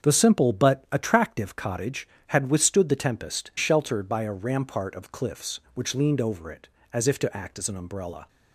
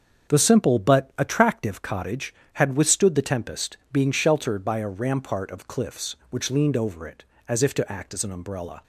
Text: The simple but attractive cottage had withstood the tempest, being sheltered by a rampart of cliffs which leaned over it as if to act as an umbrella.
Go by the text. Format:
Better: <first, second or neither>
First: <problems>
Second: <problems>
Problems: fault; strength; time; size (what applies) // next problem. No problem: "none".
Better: second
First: starts louder than the rest; until 1.1 s; 7 dB // skips "being"; at 3.5 s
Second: starts louder than the rest; until 1.3 s; 7 dB